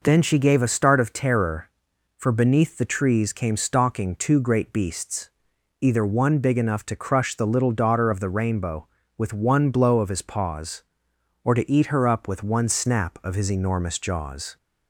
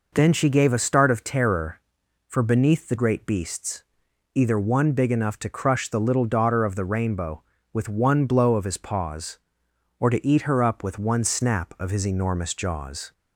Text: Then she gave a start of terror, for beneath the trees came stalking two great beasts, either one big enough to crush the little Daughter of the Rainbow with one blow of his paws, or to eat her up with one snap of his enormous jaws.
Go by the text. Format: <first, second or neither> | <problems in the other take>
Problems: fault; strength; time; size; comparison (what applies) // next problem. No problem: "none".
first | skips "trees came stalking two"; at 2.9 s